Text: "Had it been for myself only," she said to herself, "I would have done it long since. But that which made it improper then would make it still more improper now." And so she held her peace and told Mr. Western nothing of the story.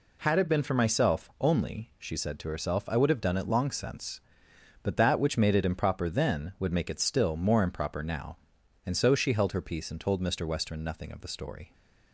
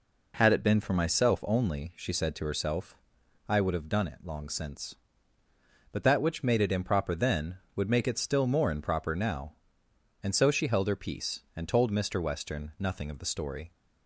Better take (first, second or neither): neither